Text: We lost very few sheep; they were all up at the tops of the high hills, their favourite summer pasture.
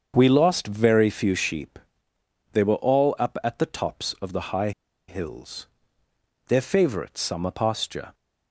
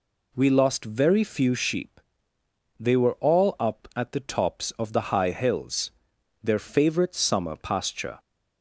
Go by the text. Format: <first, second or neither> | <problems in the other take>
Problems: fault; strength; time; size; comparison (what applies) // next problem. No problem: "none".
second | starts louder than the rest; until 1.1 s; 7 dB // pauses between "high" and "hills"; at 4.7 s; 0.37 s long